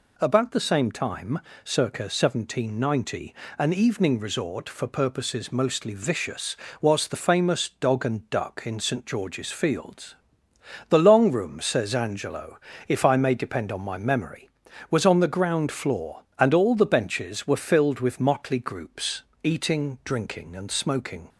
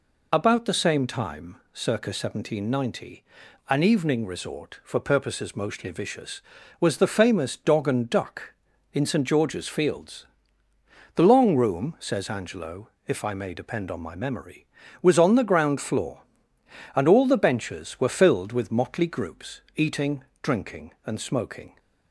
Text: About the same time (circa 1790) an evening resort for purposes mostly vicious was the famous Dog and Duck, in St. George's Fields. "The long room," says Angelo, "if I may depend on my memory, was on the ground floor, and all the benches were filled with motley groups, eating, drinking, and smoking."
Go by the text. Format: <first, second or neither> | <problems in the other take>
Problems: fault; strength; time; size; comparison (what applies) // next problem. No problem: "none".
first | loses the start of "About"; at 0.3 s; 30 ms